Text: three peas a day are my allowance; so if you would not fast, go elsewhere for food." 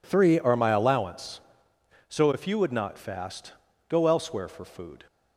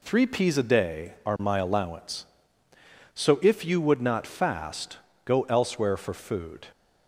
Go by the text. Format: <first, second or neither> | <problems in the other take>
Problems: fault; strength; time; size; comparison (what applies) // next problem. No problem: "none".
second | skips "peas a day"; at 0.3 s